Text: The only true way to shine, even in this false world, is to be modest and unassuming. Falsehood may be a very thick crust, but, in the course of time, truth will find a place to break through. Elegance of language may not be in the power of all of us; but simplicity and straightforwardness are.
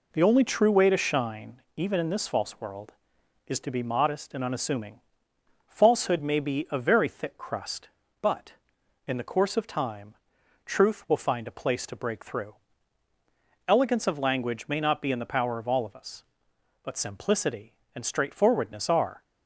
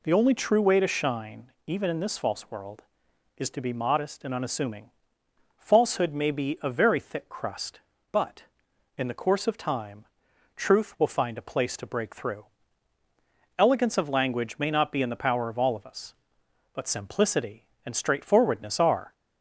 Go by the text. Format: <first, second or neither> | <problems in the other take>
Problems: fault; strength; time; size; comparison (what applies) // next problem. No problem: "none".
second | gets quieter; noticeable; throughout; 4.5 dB